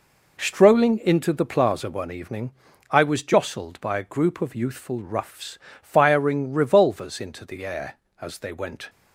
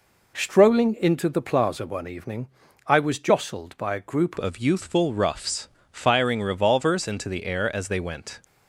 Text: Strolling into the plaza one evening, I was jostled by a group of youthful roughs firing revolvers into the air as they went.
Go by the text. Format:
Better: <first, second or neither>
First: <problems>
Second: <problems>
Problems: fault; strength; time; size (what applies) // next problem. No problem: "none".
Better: first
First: pauses between "roughs" and "firing"; slight; at 5.5 s; 0.24 s long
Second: changes voice at "of"; from 4.3 s on; 4.1 s long // pauses between "roughs" and "firing"; slight; at 5.6 s; 0.24 s long